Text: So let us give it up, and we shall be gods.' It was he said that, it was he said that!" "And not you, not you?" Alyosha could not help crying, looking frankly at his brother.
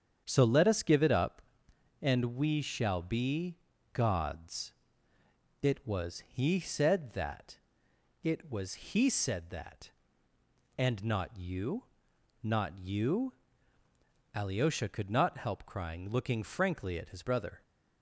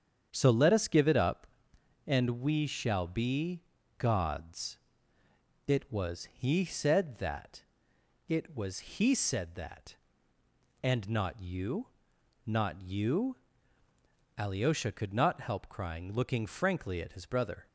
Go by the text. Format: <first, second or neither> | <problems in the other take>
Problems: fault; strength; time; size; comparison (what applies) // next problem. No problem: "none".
neither | starts louder than the rest; strong; the same in both // pauses between "be" and "gods"; slight; the same in both